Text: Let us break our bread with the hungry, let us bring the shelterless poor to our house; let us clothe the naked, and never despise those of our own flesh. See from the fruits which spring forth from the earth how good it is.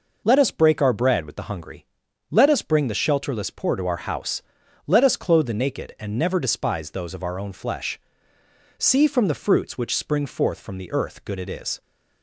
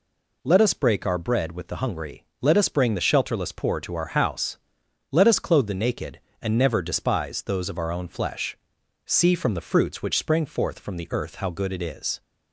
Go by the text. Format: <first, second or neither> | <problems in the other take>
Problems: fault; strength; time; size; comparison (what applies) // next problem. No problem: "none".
second | skips "how"; at 11.2 s